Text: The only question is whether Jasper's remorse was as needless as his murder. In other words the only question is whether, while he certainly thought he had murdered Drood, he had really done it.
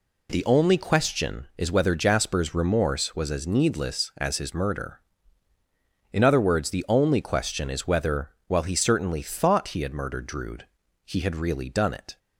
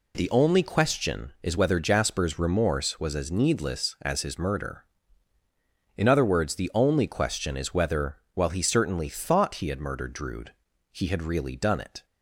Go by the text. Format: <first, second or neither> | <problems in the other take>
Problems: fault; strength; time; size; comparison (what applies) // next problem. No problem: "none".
neither | none